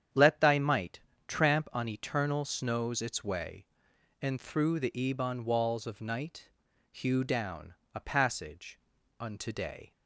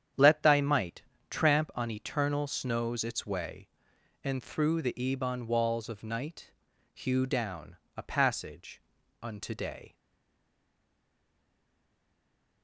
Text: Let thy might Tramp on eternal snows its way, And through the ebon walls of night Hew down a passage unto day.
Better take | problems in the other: first | starts louder than the rest; strong; until 1.4 s; 9 dB; strong in the first // pauses between "might" and "Tramp"; slight; at 1.0 s; 0.28 s long; slight in the first // pauses between "night" and "Hew"; at 6.5 s; 0.42 s long; also in the first // pauses between "down" and "a"; slight; at 7.7 s; 0.18 s long; slight in the first // pauses between "passage" and "unto"; at 8.7 s; 0.42 s long; also in the first // stays silent after the last word; strong; from 9.9 s on; 2.7 s long

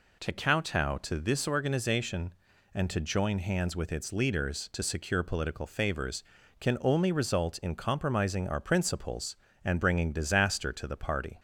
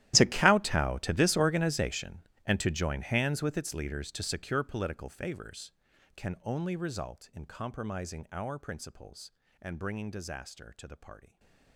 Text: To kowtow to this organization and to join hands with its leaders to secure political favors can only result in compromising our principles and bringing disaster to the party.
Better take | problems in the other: first | gets quieter; strong; throughout; 20 dB // stays silent after the last word; slight; from 11.2 s on; 0.5 s long

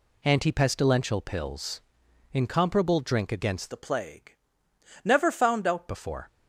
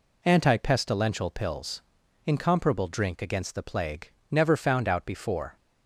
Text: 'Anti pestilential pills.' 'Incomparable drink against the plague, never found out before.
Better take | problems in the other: second | changes voice from "the" to "out"; from 3.7 to 5.8 s; 2.1 s long

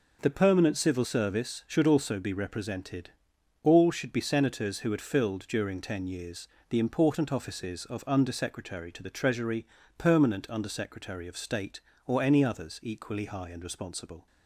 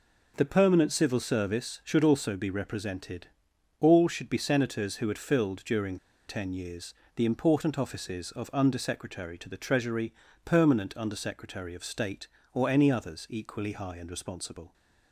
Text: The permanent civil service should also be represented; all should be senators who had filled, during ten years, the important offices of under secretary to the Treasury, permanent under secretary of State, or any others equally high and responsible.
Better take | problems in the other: first | pauses between "during" and "ten"; slight; at 5.9 s; 0.32 s long

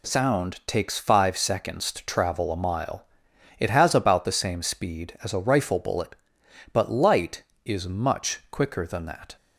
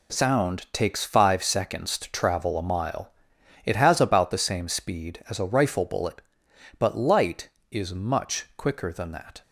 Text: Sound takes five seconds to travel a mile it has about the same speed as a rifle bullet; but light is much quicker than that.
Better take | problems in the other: first | gets quieter; strong; throughout; 9.5 dB // pauses between "mile" and "it"; noticeable; at 3.1 s; 0.54 s long; noticeable in the first

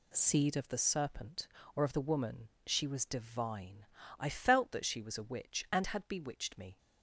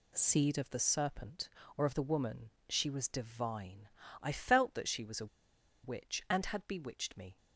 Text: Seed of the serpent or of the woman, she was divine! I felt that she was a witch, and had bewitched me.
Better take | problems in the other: first | pauses between "a" and "witch"; noticeable; at 5.2 s; 0.57 s long

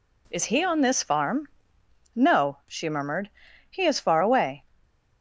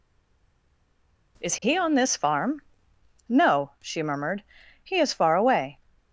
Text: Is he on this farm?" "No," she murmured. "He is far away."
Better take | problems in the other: first | stays silent before the first word; noticeable; until 1.3 s; 1.3 s long

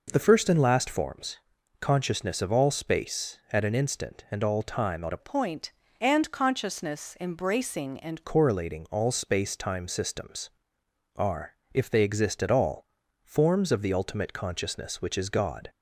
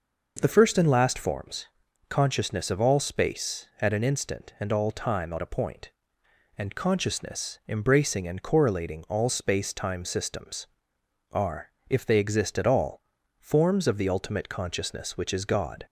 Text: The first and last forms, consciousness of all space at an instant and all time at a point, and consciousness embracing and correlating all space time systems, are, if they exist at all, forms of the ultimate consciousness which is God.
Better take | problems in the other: second | changes voice from "point" to "and"; from 5.1 to 8.2 s; 3.1 s long

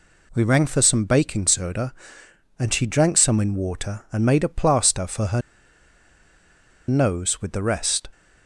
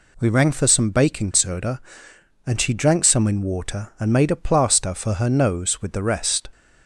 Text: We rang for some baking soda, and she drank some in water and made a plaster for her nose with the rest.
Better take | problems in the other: second | pauses between "her" and "nose"; strong; at 5.4 s; 1.4 s long

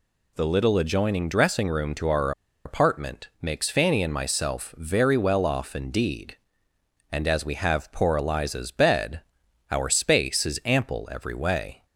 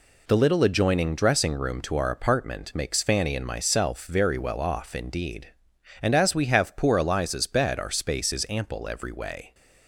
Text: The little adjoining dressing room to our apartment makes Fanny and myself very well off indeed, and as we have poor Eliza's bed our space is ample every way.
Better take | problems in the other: second | pauses between "our" and "apartment"; slight; at 2.3 s; 0.34 s long // pauses between "bed" and "our"; noticeable; at 9.2 s; 0.50 s long

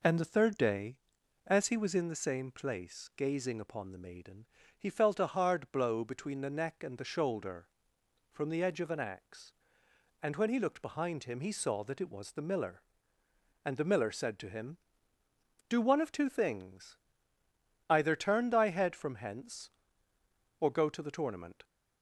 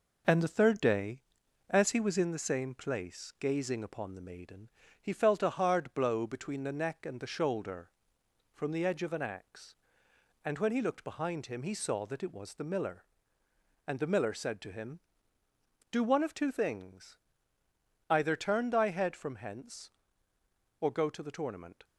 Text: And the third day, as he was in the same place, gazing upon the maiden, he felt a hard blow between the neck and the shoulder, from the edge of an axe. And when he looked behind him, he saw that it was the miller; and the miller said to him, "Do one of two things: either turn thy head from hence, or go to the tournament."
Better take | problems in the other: first | gets quieter; throughout; 3.5 dB

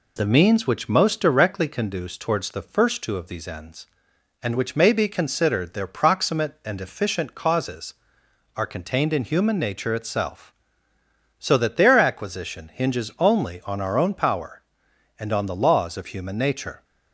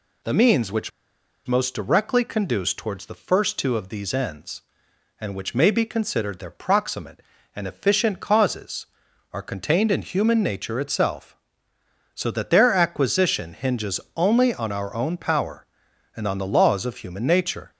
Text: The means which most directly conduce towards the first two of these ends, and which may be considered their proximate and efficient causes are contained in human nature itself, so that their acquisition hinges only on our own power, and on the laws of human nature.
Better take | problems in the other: first | pauses between "which" and "most"; noticeable; at 0.9 s; 0.56 s long // pauses between "hinges" and "only"; slight; at 14.0 s; 0.16 s long

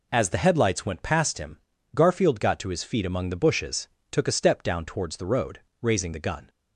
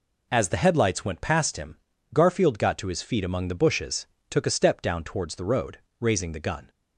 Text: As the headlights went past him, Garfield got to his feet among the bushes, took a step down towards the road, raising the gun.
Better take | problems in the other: neither | none

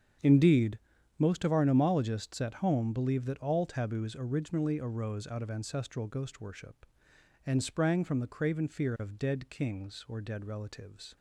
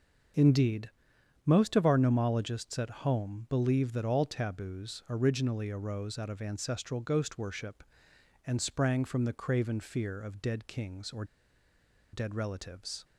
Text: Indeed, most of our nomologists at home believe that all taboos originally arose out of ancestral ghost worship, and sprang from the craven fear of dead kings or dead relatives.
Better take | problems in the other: first | starts louder than the rest; until 1.9 s; 7 dB; strong in the first // pauses between "or" and "dead"; noticeable; at 11.2 s; 0.89 s long

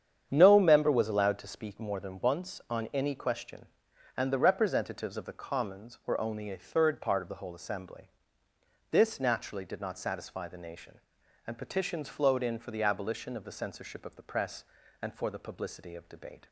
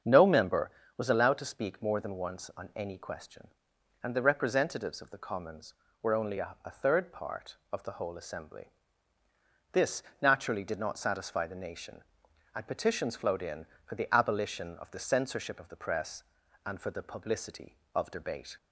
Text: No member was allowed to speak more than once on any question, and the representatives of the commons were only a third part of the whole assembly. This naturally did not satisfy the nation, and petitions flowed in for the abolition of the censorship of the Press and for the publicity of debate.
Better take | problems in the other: first | starts louder than the rest; strong; until 1.3 s; 7.5 dB; strong in the first // says "a" twice; at 6.6 s // pauses between "This" and "naturally"; slight; at 10.0 s; 0.20 s long

